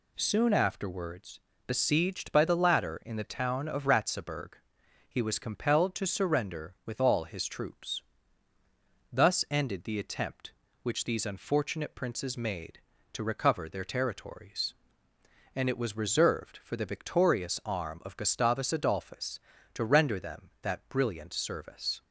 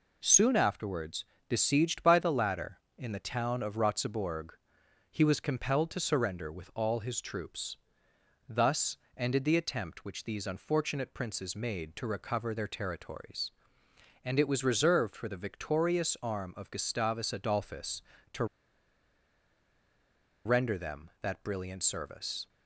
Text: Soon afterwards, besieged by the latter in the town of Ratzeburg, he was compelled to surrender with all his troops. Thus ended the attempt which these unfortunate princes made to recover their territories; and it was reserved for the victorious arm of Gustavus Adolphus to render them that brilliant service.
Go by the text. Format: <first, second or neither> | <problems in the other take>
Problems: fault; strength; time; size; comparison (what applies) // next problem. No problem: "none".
first | pauses between "Thus" and "ended"; slight; at 8.9 s; 0.20 s long // pauses between "to" and "render"; strong; at 18.4 s; 2.0 s long